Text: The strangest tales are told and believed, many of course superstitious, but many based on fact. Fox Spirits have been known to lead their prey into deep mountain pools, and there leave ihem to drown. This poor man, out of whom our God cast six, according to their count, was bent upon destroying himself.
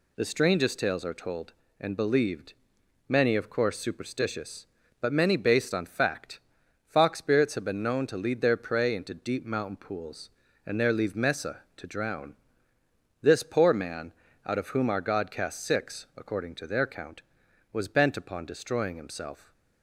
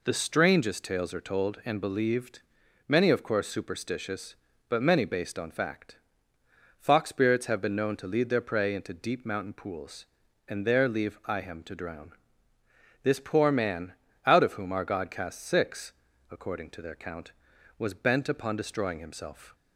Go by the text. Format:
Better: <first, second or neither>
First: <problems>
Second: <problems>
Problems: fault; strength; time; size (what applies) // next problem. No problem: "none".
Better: second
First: says "mesa" for "ihem"; at 11.1 s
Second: none